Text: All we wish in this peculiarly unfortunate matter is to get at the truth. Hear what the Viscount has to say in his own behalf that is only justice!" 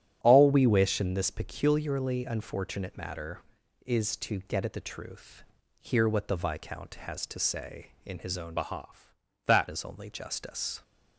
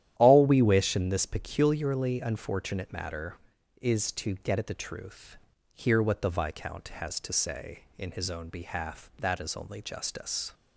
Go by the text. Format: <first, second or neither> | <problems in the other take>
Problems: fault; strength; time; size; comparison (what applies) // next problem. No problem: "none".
second | starts louder than the rest; strong; until 1.2 s; 10.5 dB; strong in the second // changes voice from "behalf" to "that"; from 8.5 to 9.6 s; 1.1 s long